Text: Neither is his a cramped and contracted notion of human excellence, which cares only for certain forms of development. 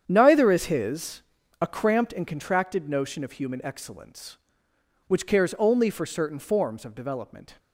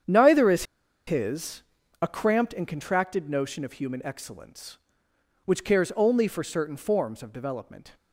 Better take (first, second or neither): first